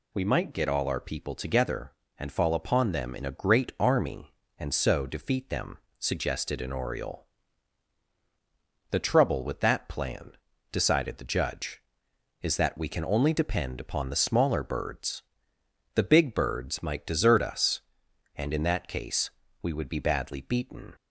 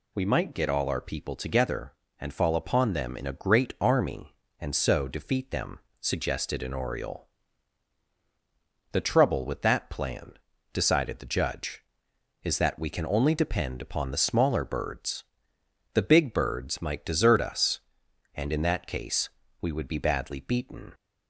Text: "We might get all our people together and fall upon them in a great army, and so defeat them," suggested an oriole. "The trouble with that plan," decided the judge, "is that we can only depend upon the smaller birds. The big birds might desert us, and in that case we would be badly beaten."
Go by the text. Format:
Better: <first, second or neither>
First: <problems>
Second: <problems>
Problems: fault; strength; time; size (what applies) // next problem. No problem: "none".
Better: neither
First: pauses between "case" and "we"; slight; at 19.2 s; 0.32 s long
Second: pauses between "case" and "we"; slight; at 19.2 s; 0.32 s long